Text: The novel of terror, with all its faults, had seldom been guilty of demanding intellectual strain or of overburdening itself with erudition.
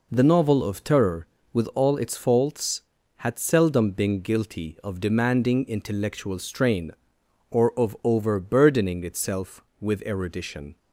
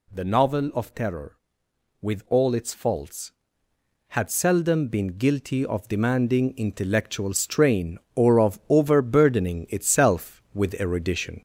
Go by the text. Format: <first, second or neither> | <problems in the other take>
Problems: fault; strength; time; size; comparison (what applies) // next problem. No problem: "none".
first | gets louder; slight; throughout; 3 dB